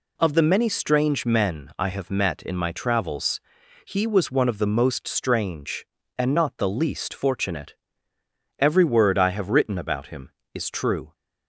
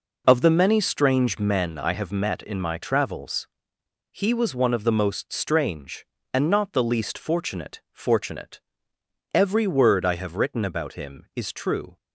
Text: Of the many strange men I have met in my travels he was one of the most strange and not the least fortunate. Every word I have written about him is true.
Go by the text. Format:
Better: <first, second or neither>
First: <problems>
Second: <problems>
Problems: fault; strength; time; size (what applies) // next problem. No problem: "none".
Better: first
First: pauses between "travels" and "he"; noticeable; at 3.4 s; 0.46 s long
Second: pauses between "travels" and "he"; noticeable; at 3.4 s; 0.64 s long // says "fortunate" twice; at 7.9 s